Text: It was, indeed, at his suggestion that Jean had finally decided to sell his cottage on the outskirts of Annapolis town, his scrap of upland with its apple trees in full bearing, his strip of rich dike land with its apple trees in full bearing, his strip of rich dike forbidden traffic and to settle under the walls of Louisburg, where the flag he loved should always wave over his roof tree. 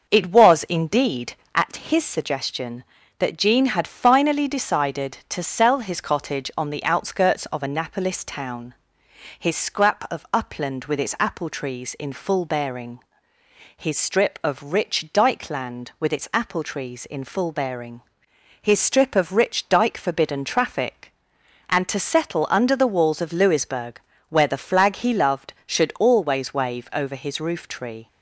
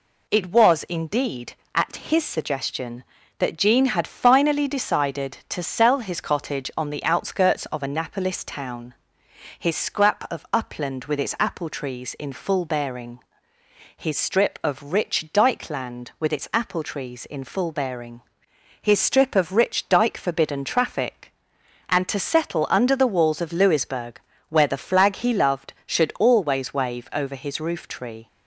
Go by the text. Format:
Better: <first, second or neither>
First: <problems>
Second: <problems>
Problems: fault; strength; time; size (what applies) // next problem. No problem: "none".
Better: second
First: starts louder than the rest; until 1.6 s; 6 dB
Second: none